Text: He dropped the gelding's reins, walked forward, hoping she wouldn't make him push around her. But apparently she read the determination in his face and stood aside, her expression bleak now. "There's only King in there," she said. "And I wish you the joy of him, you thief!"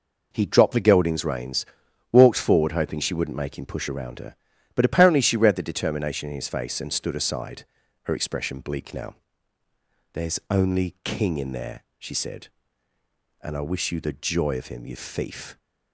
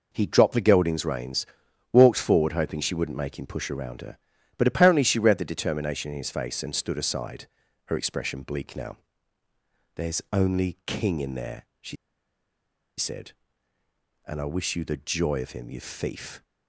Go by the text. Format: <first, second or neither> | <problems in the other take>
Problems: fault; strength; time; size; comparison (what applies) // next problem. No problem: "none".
first | pauses between "she" and "said"; at 11.9 s; 1.0 s long